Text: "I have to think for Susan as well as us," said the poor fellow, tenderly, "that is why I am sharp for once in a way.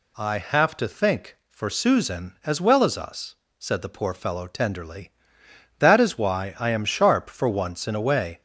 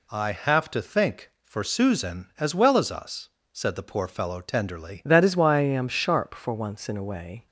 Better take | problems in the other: first | changes voice at "that"; from 5.0 s on; 2.4 s long

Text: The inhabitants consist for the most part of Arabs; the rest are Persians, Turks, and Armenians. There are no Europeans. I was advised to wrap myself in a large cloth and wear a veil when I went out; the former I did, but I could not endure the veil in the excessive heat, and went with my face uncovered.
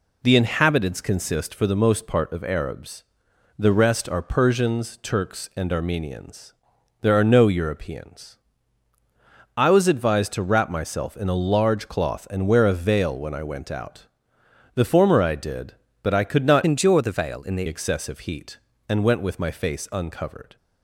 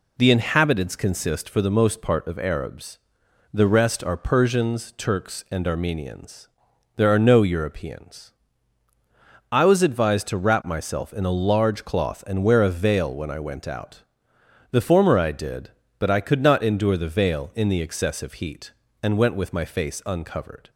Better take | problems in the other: second | changes voice from "endure" to "the"; from 16.6 to 17.6 s; 1.0 s long

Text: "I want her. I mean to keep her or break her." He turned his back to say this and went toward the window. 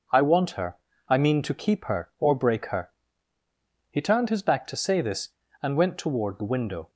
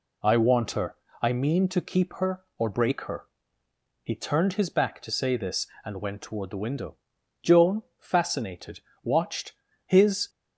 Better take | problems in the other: first | goes on to say "Joan fascinated watched his"; strong; from 7.4 s on; 2.8 s long

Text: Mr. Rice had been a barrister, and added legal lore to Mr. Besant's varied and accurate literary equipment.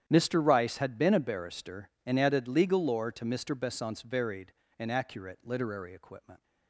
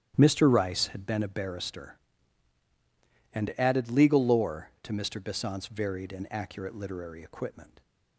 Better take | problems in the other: neither | starts louder than the rest; strong; the same in both

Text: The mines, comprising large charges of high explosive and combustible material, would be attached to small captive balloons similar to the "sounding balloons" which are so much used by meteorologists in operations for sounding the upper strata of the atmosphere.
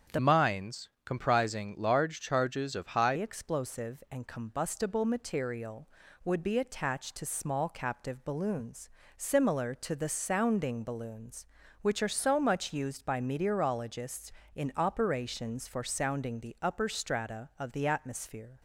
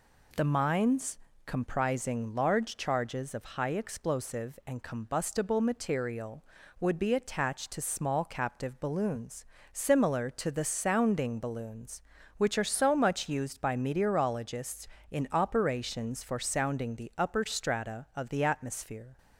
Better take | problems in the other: second | starts louder than the rest; strong; until 1.2 s; 7.5 dB // changes voice from "mines" to "high"; from 0.1 to 3.1 s; 3.0 s long // pauses between "balloons" and "similar"; slight; at 8.8 s; 0.30 s long; slight in the second

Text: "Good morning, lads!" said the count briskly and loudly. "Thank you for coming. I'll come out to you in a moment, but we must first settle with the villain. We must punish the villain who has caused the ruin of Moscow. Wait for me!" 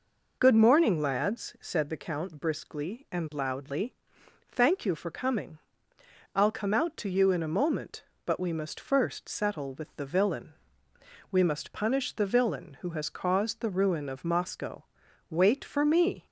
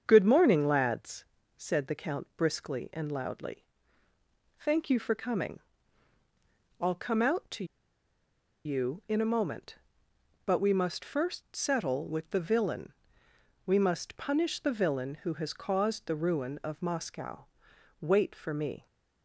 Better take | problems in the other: first | starts louder than the rest; strong; until 1.0 s; 7.5 dB // pauses between "to" and "you"; at 7.6 s; 1.0 s long

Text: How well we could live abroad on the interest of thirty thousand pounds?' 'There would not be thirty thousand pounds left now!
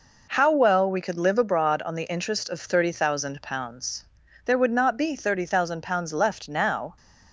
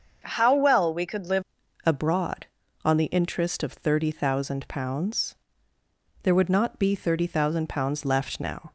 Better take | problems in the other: first | starts louder than the rest; until 1.2 s; 6.5 dB // changes voice at "abroad"; from 1.8 s on; 6.9 s long

